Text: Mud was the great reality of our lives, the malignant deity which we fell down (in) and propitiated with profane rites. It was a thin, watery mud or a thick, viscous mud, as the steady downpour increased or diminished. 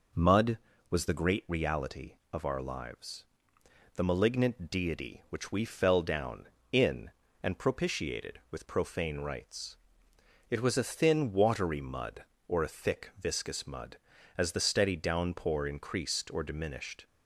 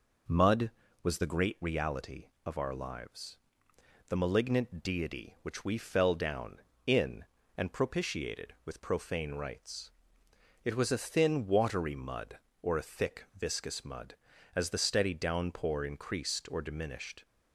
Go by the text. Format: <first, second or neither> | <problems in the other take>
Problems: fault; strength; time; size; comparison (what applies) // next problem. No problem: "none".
neither | none